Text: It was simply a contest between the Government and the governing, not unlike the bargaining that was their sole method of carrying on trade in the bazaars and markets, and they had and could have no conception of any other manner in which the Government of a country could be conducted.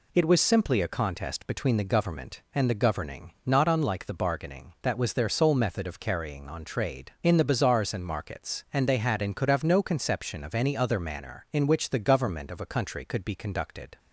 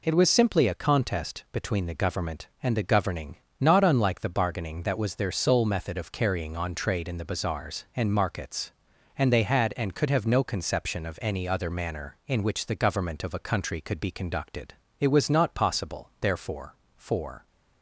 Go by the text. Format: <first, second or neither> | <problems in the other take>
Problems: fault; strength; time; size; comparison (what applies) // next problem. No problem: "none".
first | goes on to say "It was not possible therefore for"; strong; from 15.0 s on; 2.4 s long